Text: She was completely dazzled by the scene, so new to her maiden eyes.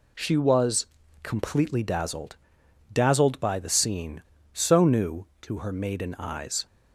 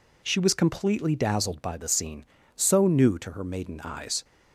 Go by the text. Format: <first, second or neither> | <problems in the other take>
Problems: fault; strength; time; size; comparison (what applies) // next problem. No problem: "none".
second | pauses between "was" and "completely"; slight; at 0.8 s; 0.34 s long // says "dazzled" twice; at 2.9 s